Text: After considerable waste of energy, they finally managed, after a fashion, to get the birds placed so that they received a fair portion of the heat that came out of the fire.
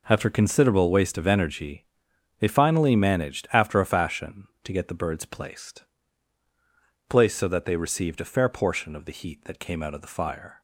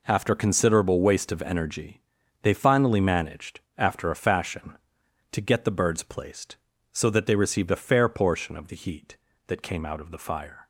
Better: second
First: says "placed" twice; at 7.0 s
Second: none

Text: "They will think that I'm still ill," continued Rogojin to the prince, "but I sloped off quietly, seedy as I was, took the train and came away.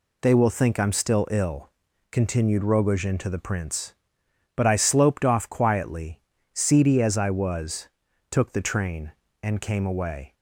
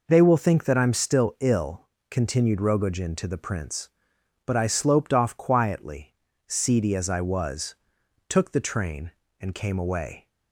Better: second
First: skips "that"; at 0.7 s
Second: none

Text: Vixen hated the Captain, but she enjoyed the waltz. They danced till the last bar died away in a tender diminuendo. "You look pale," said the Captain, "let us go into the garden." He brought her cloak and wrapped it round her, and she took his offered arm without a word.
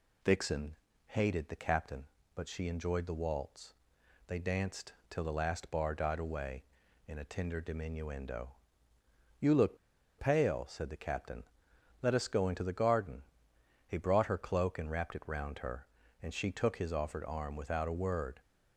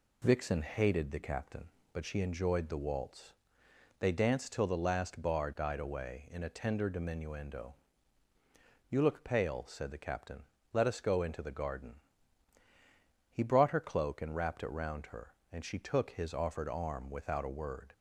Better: second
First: pauses between "Vixen" and "hated"; slight; at 0.7 s; 0.32 s long // pauses between "danced" and "till"; slight; at 4.9 s; 0.16 s long // pauses between "look" and "pale"; at 9.7 s; 0.42 s long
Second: none

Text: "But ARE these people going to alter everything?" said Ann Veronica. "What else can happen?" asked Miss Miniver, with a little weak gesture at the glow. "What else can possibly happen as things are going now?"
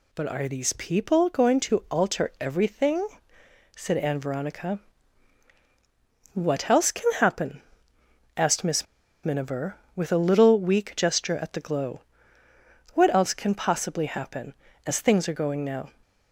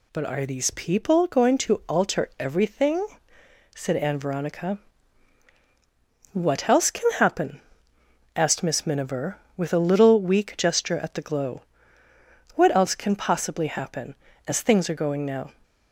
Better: second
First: pauses between "Miss" and "Miniver"; at 8.8 s; 0.37 s long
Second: none

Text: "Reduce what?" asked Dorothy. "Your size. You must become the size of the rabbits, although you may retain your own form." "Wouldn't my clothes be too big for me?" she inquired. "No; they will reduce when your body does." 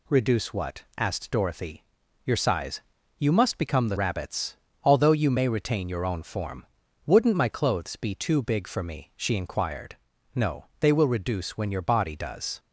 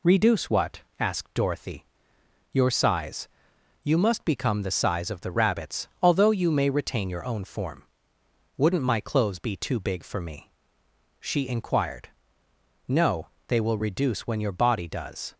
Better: second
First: skips "size of the"; at 3.9 s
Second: none

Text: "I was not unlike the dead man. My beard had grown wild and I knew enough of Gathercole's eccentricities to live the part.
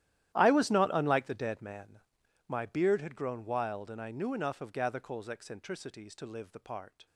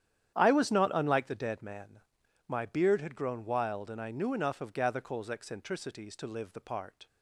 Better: second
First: gets quieter; strong; throughout; 19 dB // starts louder than the rest; strong; until 1.4 s; 13 dB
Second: starts louder than the rest; strong; until 1.4 s; 10 dB

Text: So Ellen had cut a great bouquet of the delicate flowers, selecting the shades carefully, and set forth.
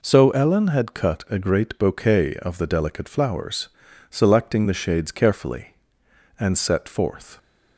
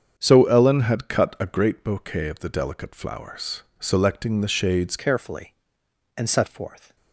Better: first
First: none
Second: starts louder than the rest; strong; until 1.1 s; 7 dB // changes voice at "carefully"; from 4.9 s on; 2.0 s long

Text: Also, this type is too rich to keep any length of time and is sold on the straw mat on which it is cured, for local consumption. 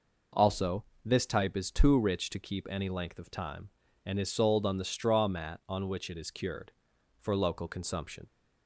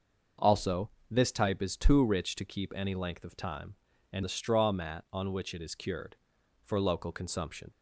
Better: first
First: none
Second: skips "is sold on"; at 4.2 s

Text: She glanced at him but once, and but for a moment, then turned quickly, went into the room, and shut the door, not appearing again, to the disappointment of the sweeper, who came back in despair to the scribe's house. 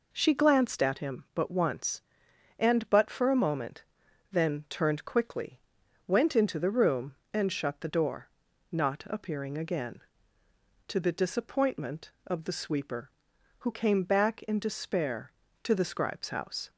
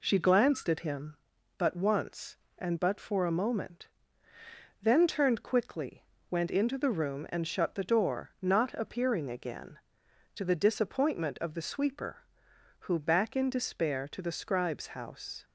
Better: first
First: none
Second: skips "came"; at 12.9 s

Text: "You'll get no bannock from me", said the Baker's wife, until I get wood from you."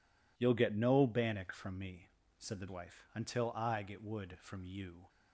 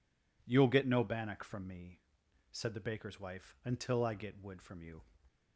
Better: second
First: skips "Baker's"; at 2.6 s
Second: none

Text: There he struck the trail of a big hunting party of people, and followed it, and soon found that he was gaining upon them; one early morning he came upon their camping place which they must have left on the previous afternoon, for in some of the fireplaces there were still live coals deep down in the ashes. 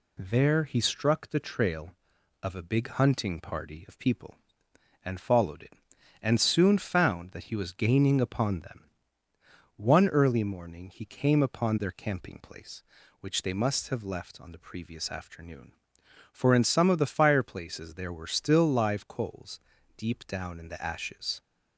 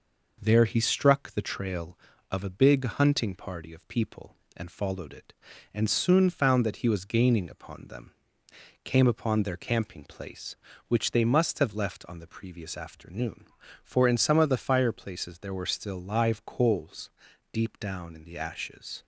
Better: first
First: pauses between "coals" and "deep"; slight; at 19.6 s; 0.34 s long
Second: skips "one early morning he"; at 8.4 s // pauses between "coals" and "deep"; at 17.1 s; 0.40 s long

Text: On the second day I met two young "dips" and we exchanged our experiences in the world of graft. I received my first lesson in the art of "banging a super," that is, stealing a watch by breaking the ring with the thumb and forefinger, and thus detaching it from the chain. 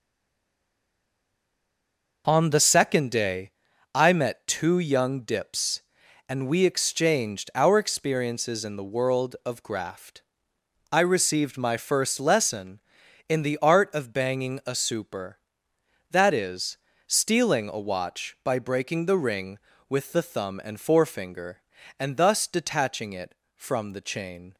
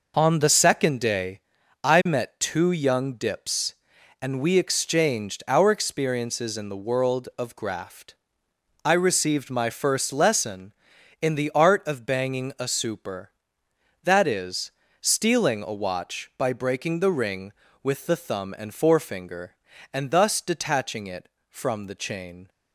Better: second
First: stays silent before the first word; until 2.2 s; 2.2 s long // pauses between "day" and "I"; at 3.5 s; 0.42 s long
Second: pauses between "day" and "I"; at 1.4 s; 0.42 s long

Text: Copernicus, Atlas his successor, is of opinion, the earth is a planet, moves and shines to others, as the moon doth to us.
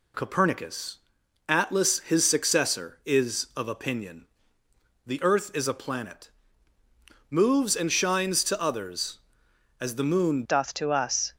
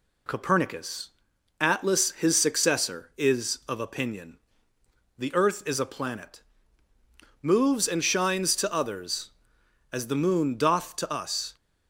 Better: second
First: changes voice at "doth"; from 10.4 s on; 0.9 s long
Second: none

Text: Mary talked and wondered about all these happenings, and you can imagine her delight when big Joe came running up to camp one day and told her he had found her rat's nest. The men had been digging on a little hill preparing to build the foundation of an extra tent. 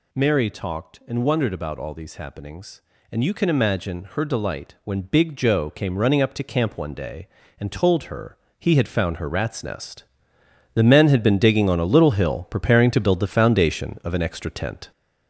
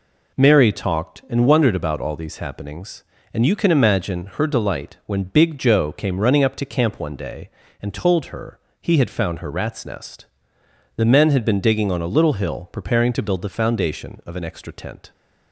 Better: second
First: gets louder; noticeable; throughout; 5.5 dB // pauses between "her" and "he"; slight; at 8.3 s; 0.24 s long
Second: pauses between "her" and "he"; slight; at 8.5 s; 0.24 s long

